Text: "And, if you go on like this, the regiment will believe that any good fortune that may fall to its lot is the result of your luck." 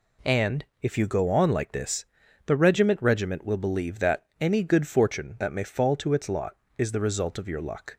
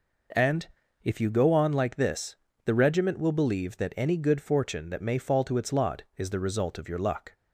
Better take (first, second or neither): second